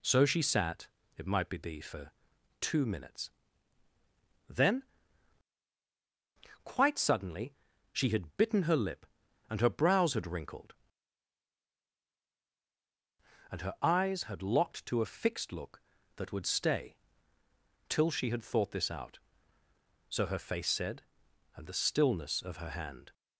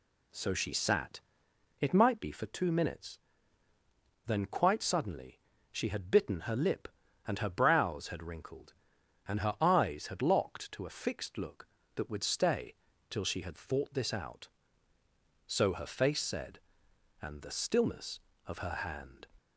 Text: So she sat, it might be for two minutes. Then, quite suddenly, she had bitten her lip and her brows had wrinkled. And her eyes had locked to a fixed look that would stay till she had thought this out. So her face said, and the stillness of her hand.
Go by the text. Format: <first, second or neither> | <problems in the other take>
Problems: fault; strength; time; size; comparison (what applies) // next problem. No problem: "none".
second | says "be" twice; at 1.5 s // pauses between "for" and "two"; noticeable; at 2.1 s; 0.48 s long // pauses between "stay" and "till"; noticeable; at 16.9 s; 0.92 s long; slight in the second